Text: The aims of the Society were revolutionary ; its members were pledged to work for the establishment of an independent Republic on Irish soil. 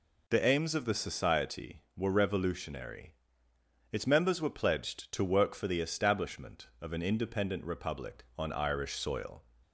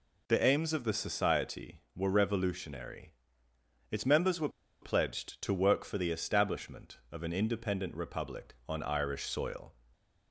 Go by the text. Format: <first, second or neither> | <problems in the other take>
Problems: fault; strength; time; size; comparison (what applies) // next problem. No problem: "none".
first | pauses between "were" and "pledged"; slight; at 4.4 s; 0.32 s long // stays silent after the last word; slight; from 9.7 s on; 0.6 s long